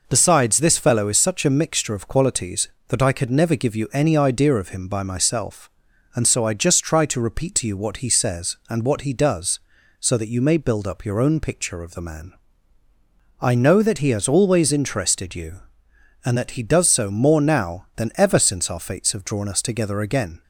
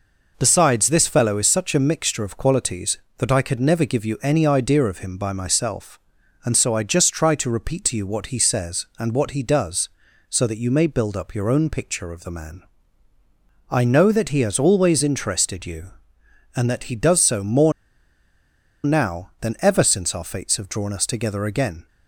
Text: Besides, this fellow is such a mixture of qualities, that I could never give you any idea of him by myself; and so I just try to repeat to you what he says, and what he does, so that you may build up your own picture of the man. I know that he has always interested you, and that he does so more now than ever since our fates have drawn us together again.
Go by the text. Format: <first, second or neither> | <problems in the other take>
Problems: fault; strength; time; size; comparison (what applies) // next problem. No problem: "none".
first | pauses between "more" and "now"; at 17.7 s; 1.1 s long